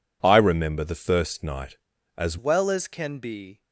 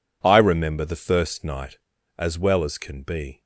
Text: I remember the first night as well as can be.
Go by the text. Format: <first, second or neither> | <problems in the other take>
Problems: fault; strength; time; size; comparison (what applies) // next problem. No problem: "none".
second | changes voice at "well"; from 2.3 s on; 1.3 s long